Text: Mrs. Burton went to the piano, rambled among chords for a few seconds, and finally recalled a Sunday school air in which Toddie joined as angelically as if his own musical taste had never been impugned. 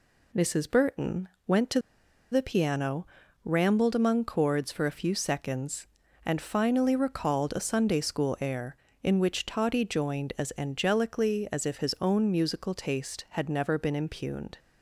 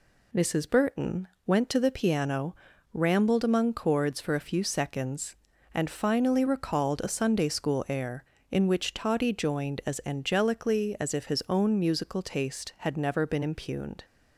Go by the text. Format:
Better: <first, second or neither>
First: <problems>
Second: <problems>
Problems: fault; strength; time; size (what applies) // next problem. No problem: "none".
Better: second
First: pauses between "Burton" and "went"; slight; at 1.2 s; 0.18 s long // pauses between "to" and "the"; noticeable; at 1.7 s; 0.51 s long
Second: pauses between "Burton" and "went"; slight; at 1.2 s; 0.18 s long